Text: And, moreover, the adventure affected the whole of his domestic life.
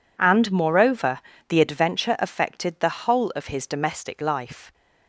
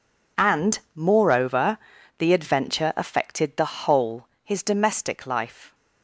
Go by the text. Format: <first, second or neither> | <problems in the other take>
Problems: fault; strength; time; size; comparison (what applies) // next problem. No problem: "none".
first | skips "of"; at 4.3 s